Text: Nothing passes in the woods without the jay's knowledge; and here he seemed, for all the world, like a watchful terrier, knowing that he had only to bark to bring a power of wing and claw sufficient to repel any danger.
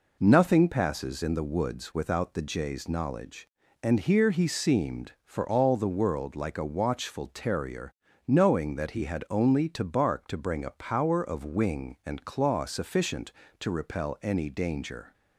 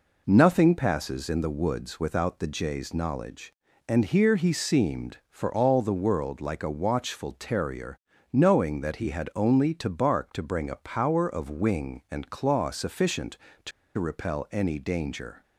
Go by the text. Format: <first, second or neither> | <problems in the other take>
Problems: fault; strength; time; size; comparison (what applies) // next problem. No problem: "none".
first | pauses between "to" and "repel"; slight; at 13.7 s; 0.27 s long